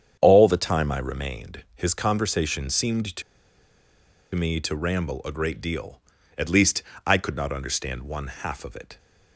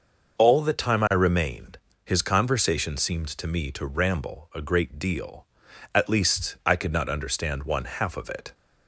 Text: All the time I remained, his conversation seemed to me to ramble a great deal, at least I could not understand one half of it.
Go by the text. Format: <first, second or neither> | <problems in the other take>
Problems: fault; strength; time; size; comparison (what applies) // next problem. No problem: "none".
second | starts louder than the rest; strong; until 1.2 s; 8 dB; noticeable in the second // pauses between "to" and "me"; at 3.2 s; 1.1 s long // pauses between "least" and "I"; slight; at 6.8 s; 0.22 s long